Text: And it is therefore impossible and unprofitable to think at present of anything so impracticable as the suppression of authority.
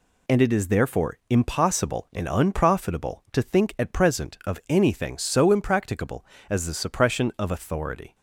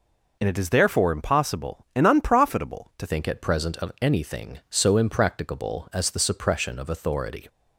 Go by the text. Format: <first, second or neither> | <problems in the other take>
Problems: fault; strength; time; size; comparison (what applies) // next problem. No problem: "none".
first | changes voice at "think"; from 3.0 s on; 4.4 s long